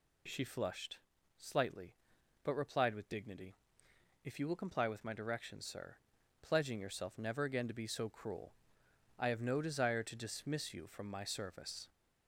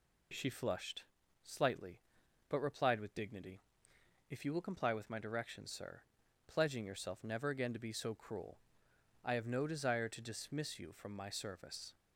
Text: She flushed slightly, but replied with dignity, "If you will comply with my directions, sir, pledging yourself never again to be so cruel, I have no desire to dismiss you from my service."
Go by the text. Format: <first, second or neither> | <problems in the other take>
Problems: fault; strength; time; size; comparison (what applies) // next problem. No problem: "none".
second | gets louder; slight; throughout; 2.5 dB // pauses between "flushed" and "slightly"; at 0.9 s; 0.38 s long; also in the second